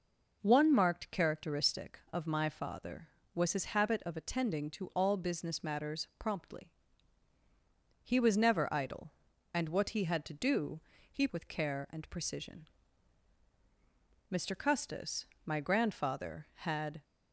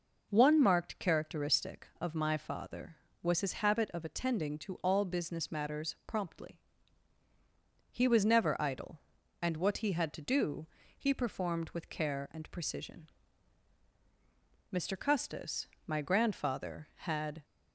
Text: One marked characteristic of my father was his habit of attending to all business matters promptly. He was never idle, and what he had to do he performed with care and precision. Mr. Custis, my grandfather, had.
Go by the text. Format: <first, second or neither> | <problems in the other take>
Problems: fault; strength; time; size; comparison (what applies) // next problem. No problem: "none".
second | pauses between "do" and "he"; slight; at 10.7 s; 0.32 s long; slight in the second // skips "performed"; at 11.2 s